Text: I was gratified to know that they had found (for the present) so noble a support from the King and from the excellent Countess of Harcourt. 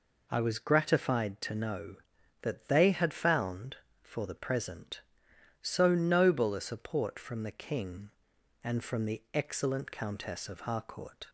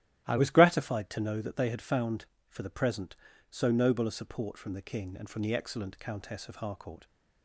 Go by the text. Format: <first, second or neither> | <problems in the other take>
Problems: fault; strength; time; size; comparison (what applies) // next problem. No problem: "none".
first | starts louder than the rest; strong; until 1.3 s; 14 dB // changes voice at "was"; from 0.3 s on; 6.7 s long